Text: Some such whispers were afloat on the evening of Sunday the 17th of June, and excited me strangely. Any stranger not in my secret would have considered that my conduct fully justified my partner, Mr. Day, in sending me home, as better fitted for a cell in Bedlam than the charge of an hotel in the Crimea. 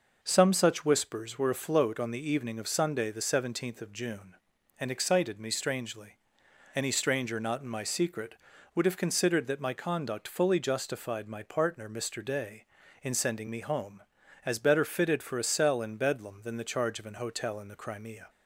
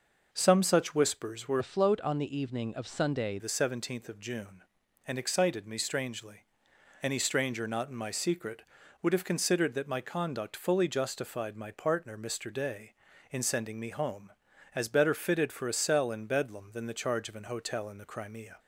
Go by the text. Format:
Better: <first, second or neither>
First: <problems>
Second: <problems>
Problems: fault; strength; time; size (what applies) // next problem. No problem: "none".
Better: first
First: none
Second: changes voice from "afloat" to "Sunday"; from 1.5 to 3.3 s; 1.8 s long